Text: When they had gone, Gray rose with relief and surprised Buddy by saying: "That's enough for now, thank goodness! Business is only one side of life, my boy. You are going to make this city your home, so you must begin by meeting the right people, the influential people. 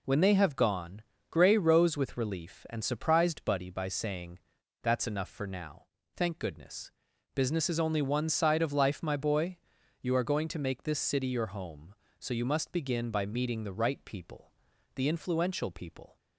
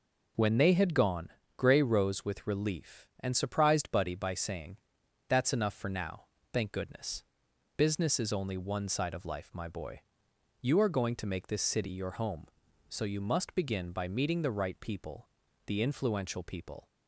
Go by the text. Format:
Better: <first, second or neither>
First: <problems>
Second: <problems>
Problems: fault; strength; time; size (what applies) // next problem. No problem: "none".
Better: second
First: says "have" for "had"; at 0.3 s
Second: none